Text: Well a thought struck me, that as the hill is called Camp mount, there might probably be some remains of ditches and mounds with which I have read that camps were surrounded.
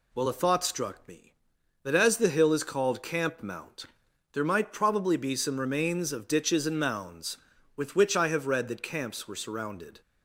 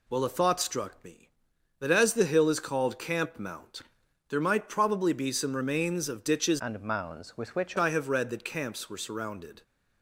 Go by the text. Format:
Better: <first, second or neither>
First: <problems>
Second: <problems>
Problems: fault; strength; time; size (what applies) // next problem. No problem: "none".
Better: first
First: none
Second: changes voice from "and" to "which"; from 6.5 to 7.7 s; 1.2 s long